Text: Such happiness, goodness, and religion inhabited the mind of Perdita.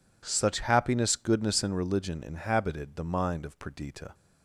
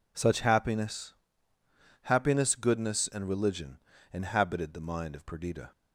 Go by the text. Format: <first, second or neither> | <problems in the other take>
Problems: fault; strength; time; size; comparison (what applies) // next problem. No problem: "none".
first | says "happiness" twice; at 2.0 s // pauses between "religion" and "inhabited"; slight; at 3.7 s; 0.34 s long